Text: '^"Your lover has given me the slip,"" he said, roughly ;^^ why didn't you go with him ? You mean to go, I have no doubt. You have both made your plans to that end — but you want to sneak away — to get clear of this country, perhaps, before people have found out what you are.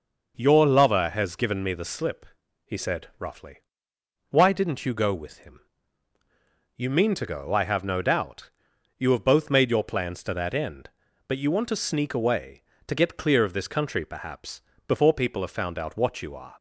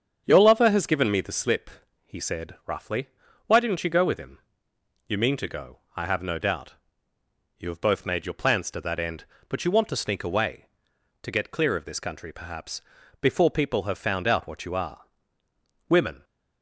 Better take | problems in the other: first | starts louder than the rest; strong; until 1.2 s; 7.5 dB // goes on to say "Women"; slight; from 15.8 s on; 0.34 s long

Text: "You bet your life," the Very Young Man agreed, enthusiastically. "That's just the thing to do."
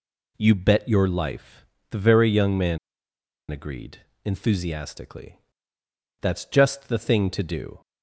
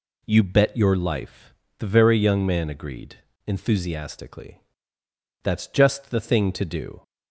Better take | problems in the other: second | pauses between "Man" and "agreed"; noticeable; at 2.7 s; 0.72 s long

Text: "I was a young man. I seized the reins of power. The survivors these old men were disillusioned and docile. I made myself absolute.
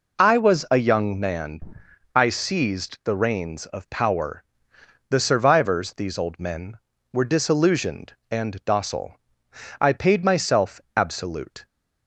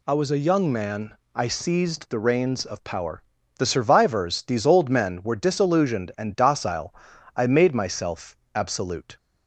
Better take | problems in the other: second | says "paid" for "made"; at 9.9 s // pauses between "myself" and "absolute"; slight; at 10.7 s; 0.16 s long; slight in the second

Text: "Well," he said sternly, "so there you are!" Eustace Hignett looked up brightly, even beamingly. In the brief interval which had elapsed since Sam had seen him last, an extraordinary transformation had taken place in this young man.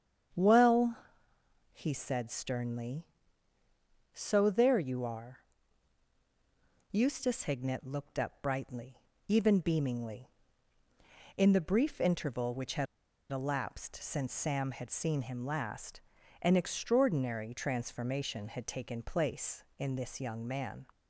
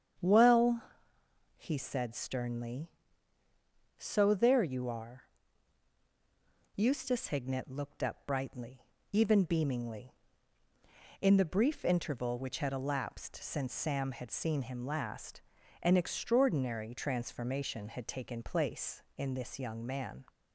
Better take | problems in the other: second | starts louder than the rest; strong; until 2.1 s; 8 dB; strong in the second // pauses between "had" and "elapsed"; at 12.8 s; 0.44 s long

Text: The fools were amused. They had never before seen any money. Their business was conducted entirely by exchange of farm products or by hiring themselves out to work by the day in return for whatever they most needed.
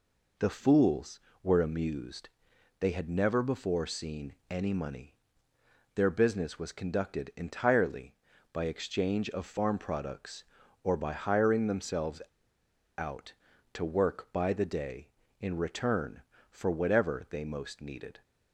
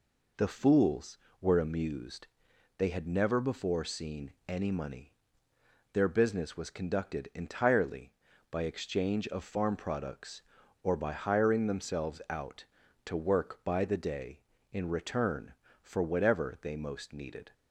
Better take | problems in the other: second | pauses between "themselves" and "out"; noticeable; at 12.2 s; 0.76 s long

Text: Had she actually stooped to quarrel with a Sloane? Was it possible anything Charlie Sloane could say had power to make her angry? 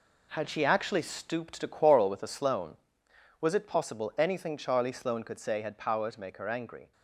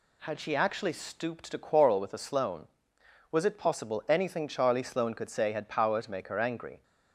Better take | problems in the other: second | gets quieter; strong; throughout; 8 dB

